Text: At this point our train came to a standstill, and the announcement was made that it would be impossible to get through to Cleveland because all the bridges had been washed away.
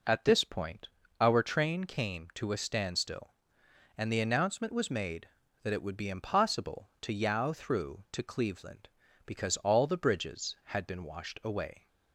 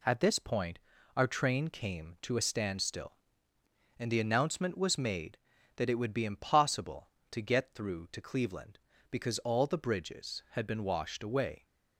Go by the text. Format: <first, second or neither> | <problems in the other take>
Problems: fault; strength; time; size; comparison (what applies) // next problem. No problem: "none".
second | pauses between "point" and "our"; slight; at 0.8 s; 0.32 s long; slight in the second // says "yow" for "get"; at 7.1 s